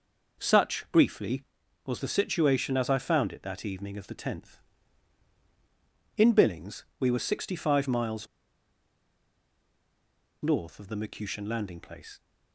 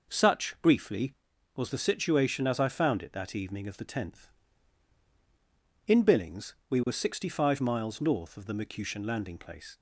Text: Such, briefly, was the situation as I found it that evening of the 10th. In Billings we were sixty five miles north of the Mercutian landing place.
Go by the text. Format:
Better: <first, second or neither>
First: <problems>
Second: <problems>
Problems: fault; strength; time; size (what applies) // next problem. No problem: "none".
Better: second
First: pauses between "miles" and "north"; strong; at 8.2 s; 2.1 s long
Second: none